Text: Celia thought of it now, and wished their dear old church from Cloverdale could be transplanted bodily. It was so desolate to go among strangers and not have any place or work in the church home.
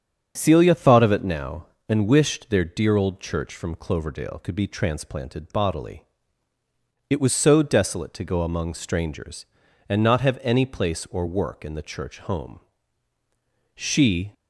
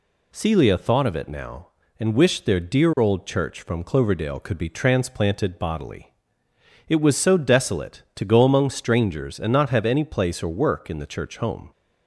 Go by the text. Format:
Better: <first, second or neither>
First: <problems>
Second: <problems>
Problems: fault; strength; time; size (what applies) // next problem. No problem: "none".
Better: second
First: starts louder than the rest; strong; until 1.3 s; 7.5 dB // goes on to say "She"; from 13.7 s on; 0.58 s long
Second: none